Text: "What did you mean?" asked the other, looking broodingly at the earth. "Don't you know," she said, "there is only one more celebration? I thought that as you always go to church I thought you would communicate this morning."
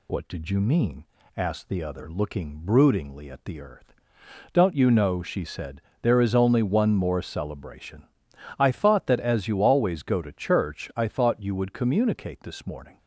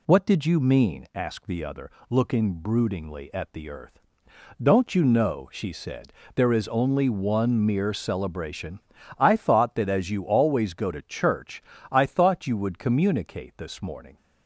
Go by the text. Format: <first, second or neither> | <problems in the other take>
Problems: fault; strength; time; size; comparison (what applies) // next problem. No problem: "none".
first | says "mere" for "more"; at 7.6 s // pauses between "church" and "I"; slight; at 11.6 s; 0.30 s long